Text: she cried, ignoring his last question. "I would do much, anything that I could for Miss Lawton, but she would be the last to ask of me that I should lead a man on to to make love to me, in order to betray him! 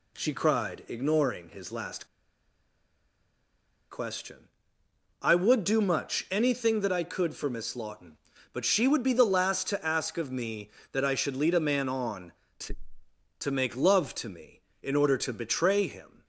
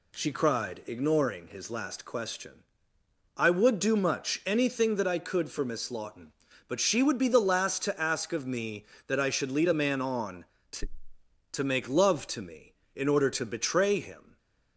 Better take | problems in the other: second | pauses between "last" and "question"; strong; at 2.0 s; 1.8 s long

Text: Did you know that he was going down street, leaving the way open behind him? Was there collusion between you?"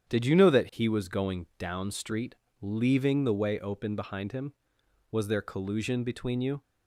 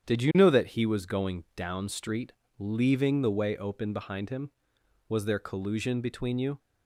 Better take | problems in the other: neither | starts louder than the rest; strong; the same in both

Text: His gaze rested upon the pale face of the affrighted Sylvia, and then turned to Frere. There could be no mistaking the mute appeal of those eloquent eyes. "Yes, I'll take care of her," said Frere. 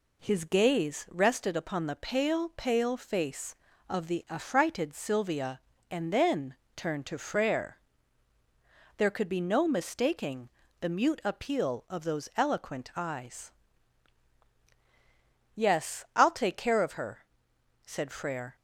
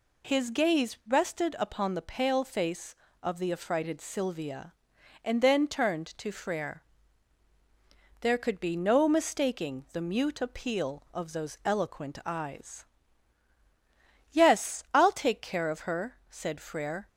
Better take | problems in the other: second | says "pale" twice; at 2.5 s // pauses between "then" and "turned"; slight; at 6.5 s; 0.22 s long // pauses between "mistaking" and "the"; slight; at 10.4 s; 0.30 s long

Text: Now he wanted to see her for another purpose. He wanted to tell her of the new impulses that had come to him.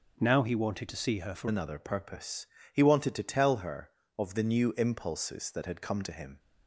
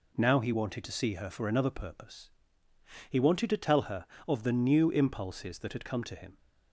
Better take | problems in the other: second | changes voice at "another"; from 1.4 s on; 4.9 s long

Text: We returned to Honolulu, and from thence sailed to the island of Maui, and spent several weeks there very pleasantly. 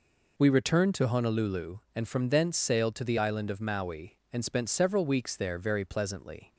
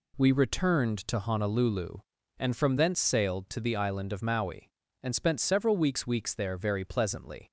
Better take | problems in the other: first | says "weeks" twice; at 6.0 s

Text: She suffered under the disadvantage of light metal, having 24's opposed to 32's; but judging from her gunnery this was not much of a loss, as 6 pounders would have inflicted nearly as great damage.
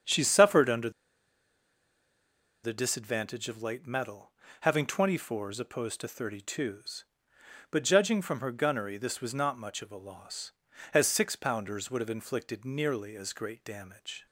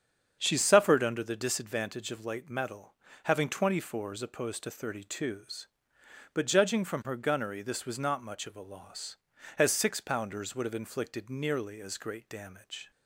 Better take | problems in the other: second | starts louder than the rest; strong; until 2.8 s; 7.5 dB; strong in the second // pauses between "under" and "the"; strong; at 0.9 s; 1.7 s long

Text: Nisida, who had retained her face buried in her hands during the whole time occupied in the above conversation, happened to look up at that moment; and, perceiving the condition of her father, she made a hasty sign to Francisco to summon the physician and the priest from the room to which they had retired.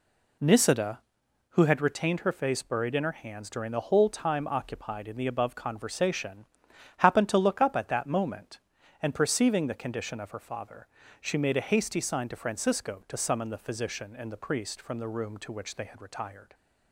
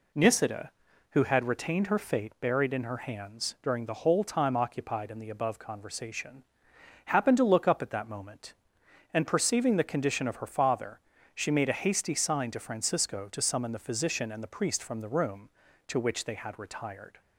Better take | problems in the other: first | says "fate" for "face"; at 1.9 s

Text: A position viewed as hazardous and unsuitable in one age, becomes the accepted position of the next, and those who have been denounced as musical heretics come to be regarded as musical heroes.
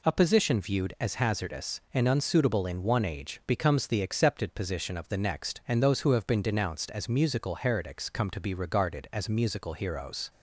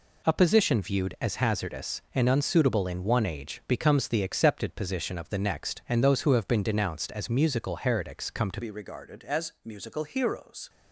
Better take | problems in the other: first | changes voice at "be"; from 8.6 s on; 2.0 s long

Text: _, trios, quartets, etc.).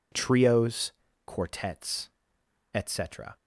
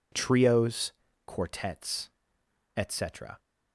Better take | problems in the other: neither | none

